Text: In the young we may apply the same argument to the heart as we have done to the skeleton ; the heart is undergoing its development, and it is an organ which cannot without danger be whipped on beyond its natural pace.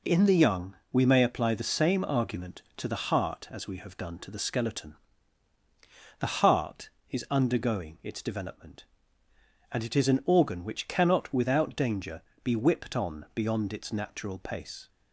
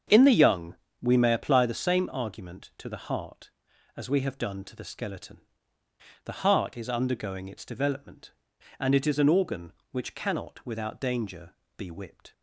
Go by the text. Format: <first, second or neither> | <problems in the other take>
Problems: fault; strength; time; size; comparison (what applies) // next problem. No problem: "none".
first | starts louder than the rest; strong; until 1.3 s; 7.5 dB // pauses between "young" and "we"; slight; at 0.7 s; 0.28 s long; slight in the first // pauses between "danger" and "be"; slight; at 11.5 s; 0.24 s long; slight in the first // stops before "on beyond its natural pace"; at 12.3 s